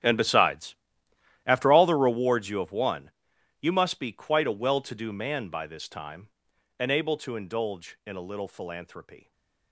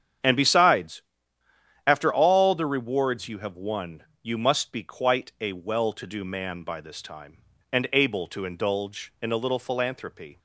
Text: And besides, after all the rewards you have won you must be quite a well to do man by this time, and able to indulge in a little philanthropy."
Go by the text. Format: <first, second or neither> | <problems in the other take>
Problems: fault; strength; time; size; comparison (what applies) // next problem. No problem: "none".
second | gets quieter; strong; throughout; 18 dB // starts louder than the rest; strong; until 1.7 s; 10 dB; strong in the second // pauses between "won" and "you"; noticeable; at 3.0 s; 0.50 s long; slight in the second // stays silent after the last word; slight; from 9.1 s on; 0.6 s long